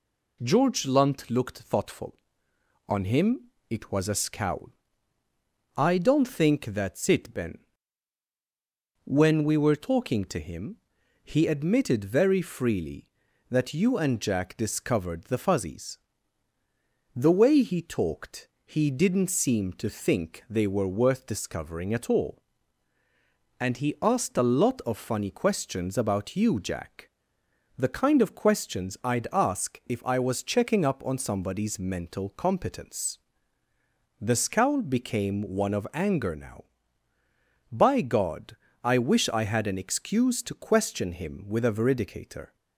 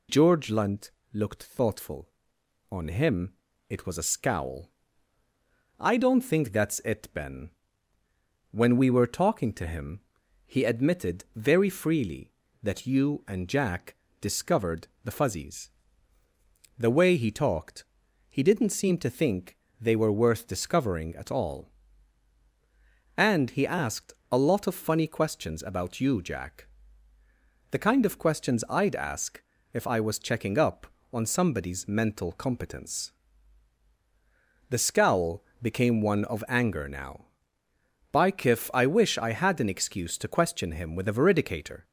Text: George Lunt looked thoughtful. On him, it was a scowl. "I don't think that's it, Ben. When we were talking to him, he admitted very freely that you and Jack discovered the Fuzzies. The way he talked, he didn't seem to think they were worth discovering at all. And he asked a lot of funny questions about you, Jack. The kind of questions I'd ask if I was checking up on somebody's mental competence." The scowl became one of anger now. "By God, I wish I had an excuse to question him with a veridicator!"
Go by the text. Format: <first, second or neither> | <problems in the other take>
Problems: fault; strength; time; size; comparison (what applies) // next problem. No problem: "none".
first | pauses between "Lunt" and "looked"; slight; at 0.8 s; 0.24 s long // pauses between "Jack" and "discovered"; slight; at 13.9 s; 0.26 s long // pauses between "discovered" and "the"; slight; at 14.8 s; 0.16 s long // pauses between "think" and "they"; slight; at 19.5 s; 0.24 s long // pauses between "asked" and "a"; slight; at 24.1 s; 0.18 s long // pauses between "ask" and "if"; slight; at 29.4 s; 0.30 s long // pauses between "scowl" and "became"; slight; at 35.4 s; 0.18 s long // says "Kiff" for "God"; at 38.3 s